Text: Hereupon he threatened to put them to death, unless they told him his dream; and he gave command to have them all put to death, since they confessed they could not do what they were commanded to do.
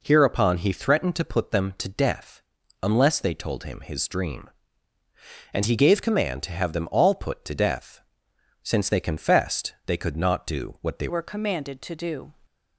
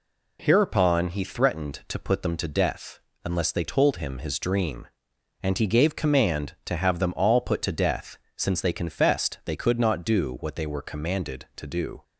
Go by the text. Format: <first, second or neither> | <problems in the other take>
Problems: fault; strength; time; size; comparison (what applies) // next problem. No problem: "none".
second | changes voice at "were"; from 11.0 s on; 1.3 s long